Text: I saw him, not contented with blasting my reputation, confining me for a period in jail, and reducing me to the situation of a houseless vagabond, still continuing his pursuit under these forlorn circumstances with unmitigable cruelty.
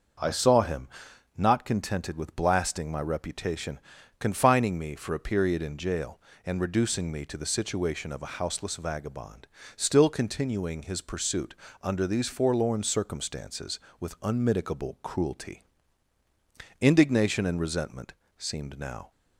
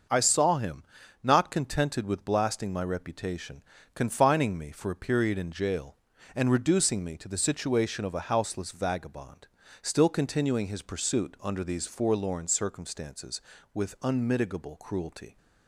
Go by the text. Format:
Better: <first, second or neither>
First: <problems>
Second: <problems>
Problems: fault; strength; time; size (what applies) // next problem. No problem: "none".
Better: second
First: starts louder than the rest; until 1.7 s; 6.5 dB // pauses between "pursuit" and "under"; slight; at 11.5 s; 0.28 s long // goes on to say "Indignation and resentment seemed now"; strong; from 16.8 s on; 2.3 s long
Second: starts louder than the rest; until 1.5 s; 6.5 dB